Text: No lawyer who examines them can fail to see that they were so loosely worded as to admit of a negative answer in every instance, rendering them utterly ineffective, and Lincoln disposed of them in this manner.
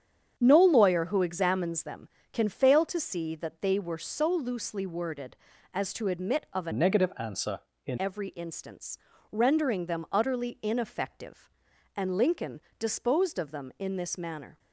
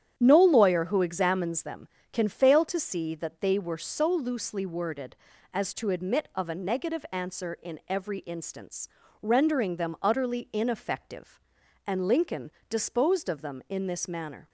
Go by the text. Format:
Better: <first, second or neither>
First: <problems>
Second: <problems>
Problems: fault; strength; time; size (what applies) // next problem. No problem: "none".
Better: second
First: starts louder than the rest; strong; until 1.3 s; 8 dB // changes voice from "negative" to "in"; from 6.7 to 7.9 s; 1.2 s long // pauses between "Lincoln" and "disposed"; slight; at 12.6 s; 0.18 s long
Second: starts louder than the rest; strong; until 1.1 s; 9 dB // pauses between "Lincoln" and "disposed"; slight; at 12.5 s; 0.18 s long